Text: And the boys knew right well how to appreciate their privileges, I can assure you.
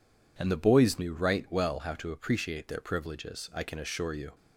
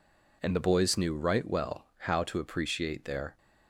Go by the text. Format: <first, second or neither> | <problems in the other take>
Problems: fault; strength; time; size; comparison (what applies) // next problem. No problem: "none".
first | stops before "privileges I can assure you"; at 3.3 s